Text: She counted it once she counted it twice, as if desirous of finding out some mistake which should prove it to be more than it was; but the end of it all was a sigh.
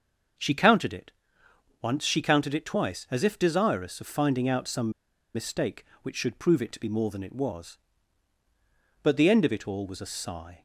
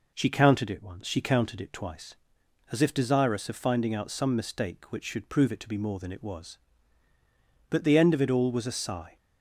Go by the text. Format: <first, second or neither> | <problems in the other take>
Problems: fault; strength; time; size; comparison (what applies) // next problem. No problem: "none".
second | starts louder than the rest; until 2.0 s; 6.5 dB // pauses between "it" and "once"; noticeable; at 1.1 s; 0.68 s long // pauses between "some" and "mistake"; at 4.8 s; 0.45 s long